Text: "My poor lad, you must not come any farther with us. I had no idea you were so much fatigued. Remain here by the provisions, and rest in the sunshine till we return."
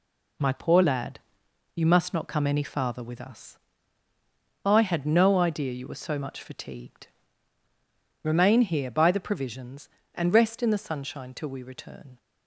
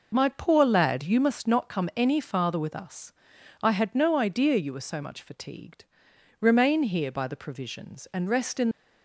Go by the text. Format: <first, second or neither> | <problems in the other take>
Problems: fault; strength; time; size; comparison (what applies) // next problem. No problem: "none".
first | stops before "the sunshine till we return"; at 8.7 s